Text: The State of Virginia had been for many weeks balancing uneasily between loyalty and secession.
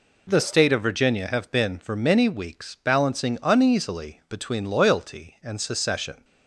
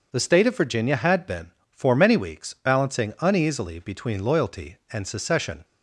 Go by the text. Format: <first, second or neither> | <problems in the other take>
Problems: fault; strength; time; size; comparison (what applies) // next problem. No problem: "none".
second | says "have" for "had"; at 1.2 s